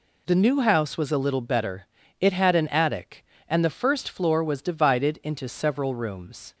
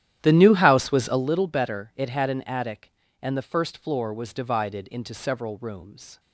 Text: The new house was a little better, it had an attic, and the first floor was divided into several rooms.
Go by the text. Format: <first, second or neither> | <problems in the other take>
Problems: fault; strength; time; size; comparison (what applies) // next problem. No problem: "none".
first | starts louder than the rest; strong; until 1.3 s; 11 dB